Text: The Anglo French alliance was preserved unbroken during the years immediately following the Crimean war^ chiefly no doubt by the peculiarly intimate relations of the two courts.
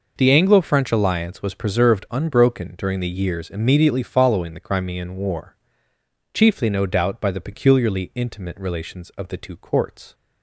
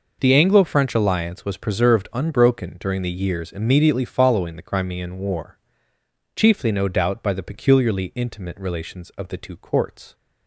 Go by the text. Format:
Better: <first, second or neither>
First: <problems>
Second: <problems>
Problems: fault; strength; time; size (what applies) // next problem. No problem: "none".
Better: neither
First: pauses between "war" and "chiefly"; noticeable; at 5.5 s; 0.80 s long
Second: pauses between "war" and "chiefly"; noticeable; at 5.5 s; 0.80 s long